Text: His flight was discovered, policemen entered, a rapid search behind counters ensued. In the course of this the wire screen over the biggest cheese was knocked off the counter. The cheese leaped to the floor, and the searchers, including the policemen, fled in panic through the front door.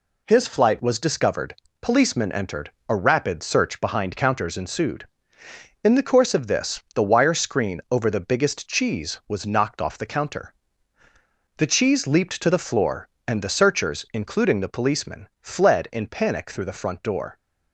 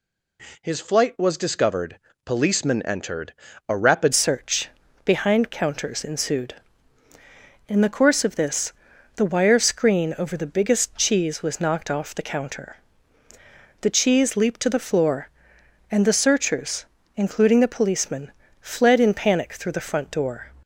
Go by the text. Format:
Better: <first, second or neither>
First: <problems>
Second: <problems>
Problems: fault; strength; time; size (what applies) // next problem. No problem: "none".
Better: first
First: none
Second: changes voice at "search"; from 4.1 s on; 16.4 s long // pauses between "search" and "behind"; slight; at 4.6 s; 0.34 s long // pauses between "this" and "the"; noticeable; at 8.7 s; 0.46 s long